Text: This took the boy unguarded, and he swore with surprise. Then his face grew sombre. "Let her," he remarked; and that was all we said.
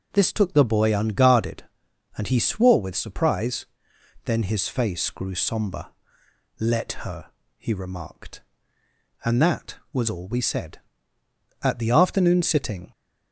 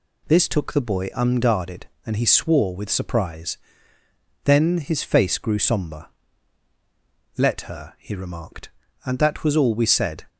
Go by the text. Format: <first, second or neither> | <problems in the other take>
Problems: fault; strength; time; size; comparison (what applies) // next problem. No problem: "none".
second | goes on to say "At the afternoon sitting"; noticeable; from 11.6 s on; 1.3 s long